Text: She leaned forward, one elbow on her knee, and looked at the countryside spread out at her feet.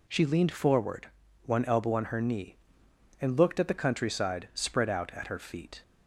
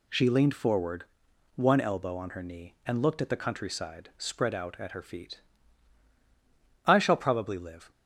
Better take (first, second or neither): first